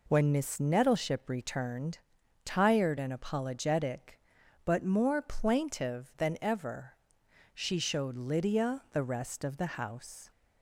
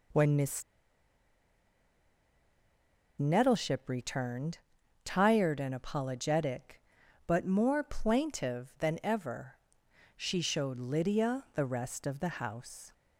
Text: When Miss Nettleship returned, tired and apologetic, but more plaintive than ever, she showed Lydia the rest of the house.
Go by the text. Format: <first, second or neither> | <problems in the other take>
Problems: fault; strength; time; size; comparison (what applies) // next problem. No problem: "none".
first | pauses between "Miss" and "Nettleship"; strong; at 0.6 s; 2.5 s long